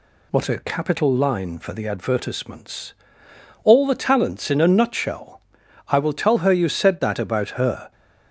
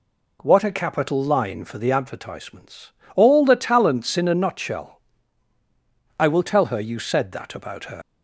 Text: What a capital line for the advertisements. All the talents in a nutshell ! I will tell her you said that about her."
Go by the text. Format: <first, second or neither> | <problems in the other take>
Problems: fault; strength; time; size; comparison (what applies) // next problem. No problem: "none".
first | leaves "her" unfinished; at 8.0 s; 85 ms